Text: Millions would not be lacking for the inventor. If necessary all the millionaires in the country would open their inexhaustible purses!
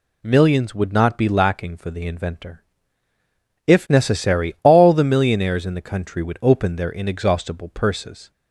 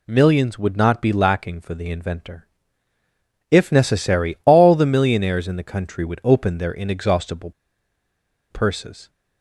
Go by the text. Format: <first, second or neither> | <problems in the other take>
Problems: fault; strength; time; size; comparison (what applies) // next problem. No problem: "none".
first | pauses between "inexhaustible" and "purses"; at 7.5 s; 0.99 s long